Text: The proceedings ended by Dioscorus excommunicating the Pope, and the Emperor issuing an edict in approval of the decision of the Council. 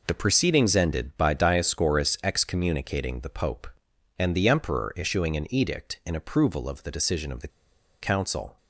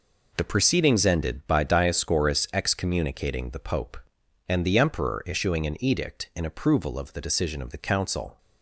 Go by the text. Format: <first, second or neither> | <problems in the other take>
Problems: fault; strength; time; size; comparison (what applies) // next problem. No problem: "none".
second | pauses between "the" and "Council"; noticeable; at 7.4 s; 0.53 s long